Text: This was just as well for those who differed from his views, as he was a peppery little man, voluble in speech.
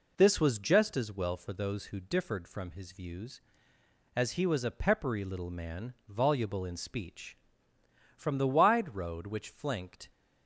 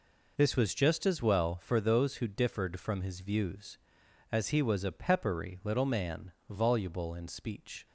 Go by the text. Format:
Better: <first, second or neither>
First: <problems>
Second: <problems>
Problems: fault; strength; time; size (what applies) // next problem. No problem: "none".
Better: second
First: goes on to say "From the wide road which flanked"; strong; from 8.1 s on; 1.9 s long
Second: none